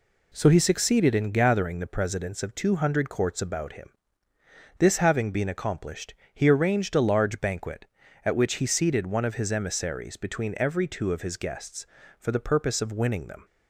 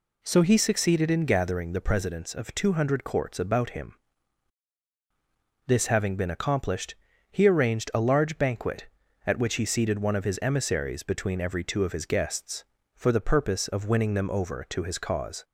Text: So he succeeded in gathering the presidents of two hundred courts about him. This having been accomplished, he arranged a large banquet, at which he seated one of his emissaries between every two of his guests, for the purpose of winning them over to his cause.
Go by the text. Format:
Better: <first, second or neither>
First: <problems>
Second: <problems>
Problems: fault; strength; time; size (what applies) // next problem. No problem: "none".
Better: second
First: stops before "over to his cause"; at 13.4 s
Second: none